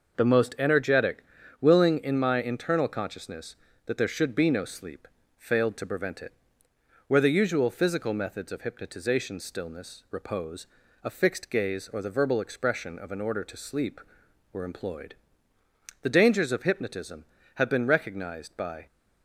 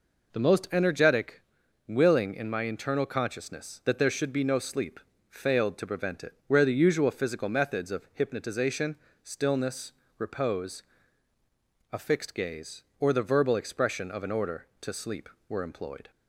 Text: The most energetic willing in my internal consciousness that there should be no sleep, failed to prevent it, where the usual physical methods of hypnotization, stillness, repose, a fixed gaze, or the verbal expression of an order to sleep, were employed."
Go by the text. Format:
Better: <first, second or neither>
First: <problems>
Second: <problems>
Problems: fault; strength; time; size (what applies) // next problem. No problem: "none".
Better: second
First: pauses between "energetic" and "willing"; slight; at 1.2 s; 0.36 s long // goes on to say "The dangers of hypnotism have been recognized by"; strong; from 16.0 s on; 2.8 s long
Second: pauses between "energetic" and "willing"; noticeable; at 1.4 s; 0.46 s long